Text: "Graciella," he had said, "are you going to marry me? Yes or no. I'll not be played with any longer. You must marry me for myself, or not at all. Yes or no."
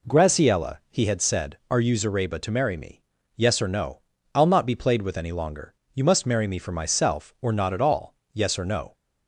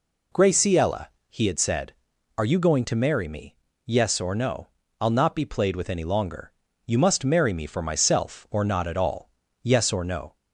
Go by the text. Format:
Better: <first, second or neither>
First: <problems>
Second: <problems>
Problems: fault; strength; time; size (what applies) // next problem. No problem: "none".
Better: second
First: says "zareba" for "going"; at 1.9 s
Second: none